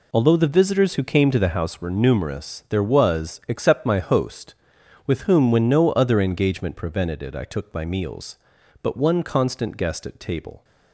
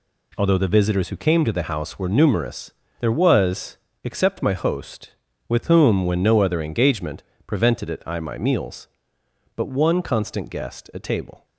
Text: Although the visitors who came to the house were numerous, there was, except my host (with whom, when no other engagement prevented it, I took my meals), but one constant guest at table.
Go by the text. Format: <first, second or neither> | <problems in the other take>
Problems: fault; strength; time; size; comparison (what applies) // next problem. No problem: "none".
first | pauses between "engagement" and "prevented"; slight; at 7.2 s; 0.24 s long // skips "took"; at 8.1 s